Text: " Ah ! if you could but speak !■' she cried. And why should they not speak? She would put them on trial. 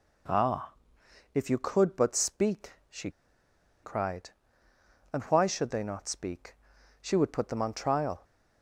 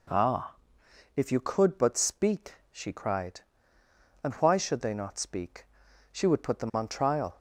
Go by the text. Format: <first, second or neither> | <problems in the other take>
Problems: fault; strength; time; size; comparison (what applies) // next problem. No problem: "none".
second | pauses between "she" and "cried"; noticeable; at 3.1 s; 0.71 s long